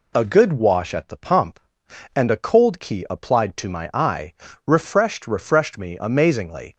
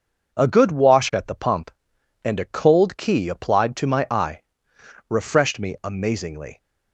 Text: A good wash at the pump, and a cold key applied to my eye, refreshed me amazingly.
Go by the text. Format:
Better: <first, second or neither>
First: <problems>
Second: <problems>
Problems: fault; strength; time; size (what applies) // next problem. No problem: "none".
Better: second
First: says "refreshed" twice; at 5.2 s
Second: none